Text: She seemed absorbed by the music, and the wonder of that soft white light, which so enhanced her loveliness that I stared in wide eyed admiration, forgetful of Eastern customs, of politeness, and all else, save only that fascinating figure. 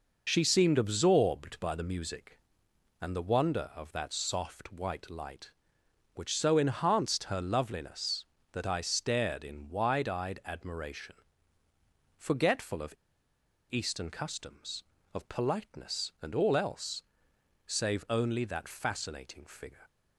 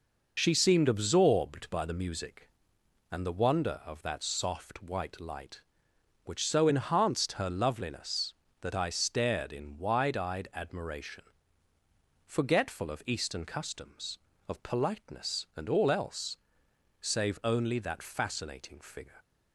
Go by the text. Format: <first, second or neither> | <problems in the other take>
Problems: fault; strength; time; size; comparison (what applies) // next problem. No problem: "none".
second | pauses between "of" and "Eastern"; noticeable; at 12.9 s; 0.77 s long